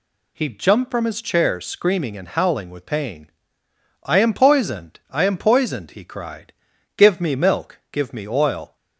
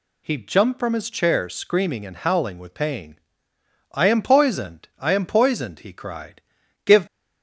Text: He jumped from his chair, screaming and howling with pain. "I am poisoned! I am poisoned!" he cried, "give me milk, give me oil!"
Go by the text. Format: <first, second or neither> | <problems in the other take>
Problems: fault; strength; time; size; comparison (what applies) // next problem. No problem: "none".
first | stops before "me milk give me oil"; at 7.0 s